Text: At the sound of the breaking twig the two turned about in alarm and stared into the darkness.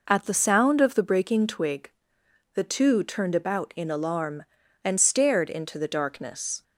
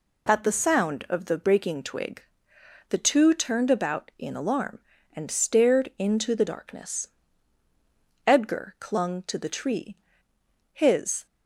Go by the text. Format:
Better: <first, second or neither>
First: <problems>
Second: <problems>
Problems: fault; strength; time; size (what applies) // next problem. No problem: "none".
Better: first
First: pauses between "twig" and "the"; noticeable; at 1.9 s; 0.64 s long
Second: pauses between "twig" and "the"; noticeable; at 2.2 s; 0.68 s long // goes on to say "Edgar clung to the tree his"; strong; from 8.2 s on; 3.0 s long